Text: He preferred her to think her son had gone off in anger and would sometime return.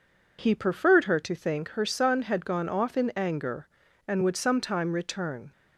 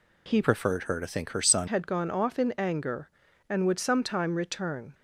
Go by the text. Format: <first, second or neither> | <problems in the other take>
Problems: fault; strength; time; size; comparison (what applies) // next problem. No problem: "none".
first | changes voice from "preferred" to "son"; from 0.4 to 1.6 s; 1.2 s long